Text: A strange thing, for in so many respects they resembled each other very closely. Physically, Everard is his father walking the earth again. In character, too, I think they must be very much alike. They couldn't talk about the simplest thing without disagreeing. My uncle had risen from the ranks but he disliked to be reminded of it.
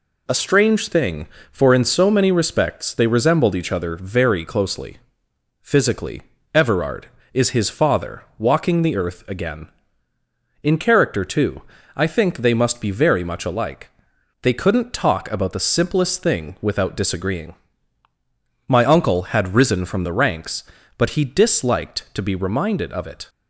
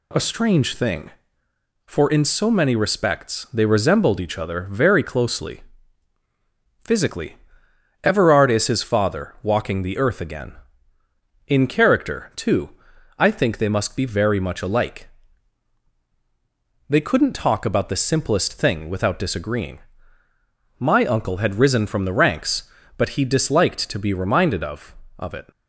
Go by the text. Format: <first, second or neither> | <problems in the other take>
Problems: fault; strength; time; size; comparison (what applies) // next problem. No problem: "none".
first | says "of" twice; at 25.2 s